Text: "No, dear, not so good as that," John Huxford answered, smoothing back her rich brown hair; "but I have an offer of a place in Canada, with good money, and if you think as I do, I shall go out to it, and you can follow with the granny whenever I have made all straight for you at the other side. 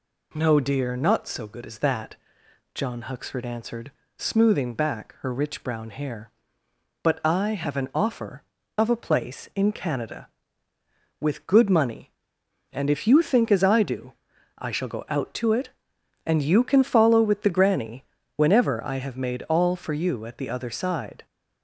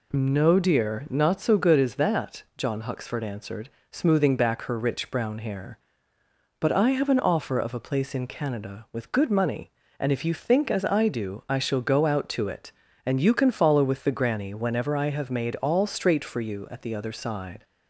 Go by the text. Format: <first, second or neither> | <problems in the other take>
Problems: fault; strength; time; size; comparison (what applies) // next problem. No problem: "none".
second | pauses between "granny" and "whenever"; slight; at 18.0 s; 0.32 s long // skips "straight"; at 19.7 s